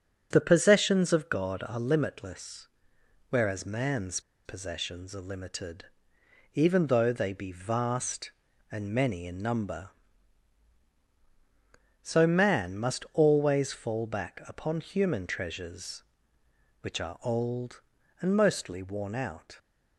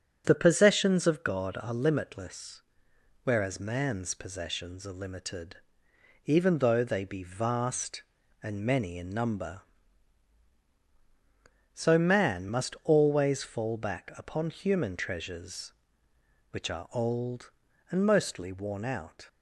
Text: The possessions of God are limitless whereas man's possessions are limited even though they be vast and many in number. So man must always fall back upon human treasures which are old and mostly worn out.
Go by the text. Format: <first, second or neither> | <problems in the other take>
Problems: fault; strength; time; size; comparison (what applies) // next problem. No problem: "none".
second | starts louder than the rest; until 1.3 s; 7 dB; strong in the second // pauses between "limitless" and "whereas"; noticeable; at 2.6 s; 0.60 s long; noticeable in the second // pauses between "man's" and "possessions"; slight; at 4.1 s; 0.25 s long // pauses between "limited" and "even"; noticeable; at 5.8 s; 0.68 s long; noticeable in the second